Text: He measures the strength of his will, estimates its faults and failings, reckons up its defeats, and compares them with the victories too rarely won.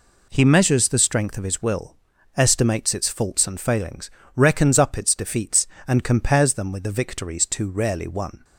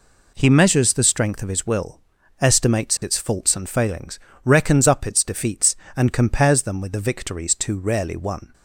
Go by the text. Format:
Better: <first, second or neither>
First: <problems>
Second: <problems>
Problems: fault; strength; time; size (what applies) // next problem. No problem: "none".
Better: neither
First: none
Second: none